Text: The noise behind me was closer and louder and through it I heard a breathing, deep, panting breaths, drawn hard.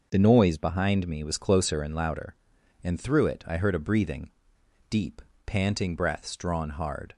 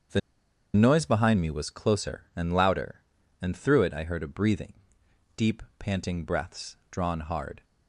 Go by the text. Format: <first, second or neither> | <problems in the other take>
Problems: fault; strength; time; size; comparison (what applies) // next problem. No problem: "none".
first | starts louder than the rest; strong; until 1.6 s; 7 dB // pauses between "The" and "noise"; noticeable; at 0.2 s; 0.55 s long